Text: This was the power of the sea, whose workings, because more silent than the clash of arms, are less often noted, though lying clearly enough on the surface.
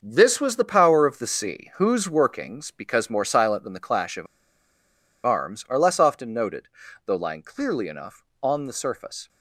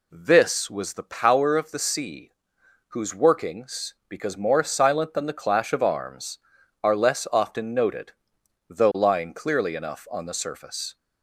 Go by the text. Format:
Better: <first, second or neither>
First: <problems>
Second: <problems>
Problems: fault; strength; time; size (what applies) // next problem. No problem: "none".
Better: second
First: starts louder than the rest; until 1.0 s; 6.5 dB // pauses between "of" and "arms"; at 4.2 s; 0.99 s long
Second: none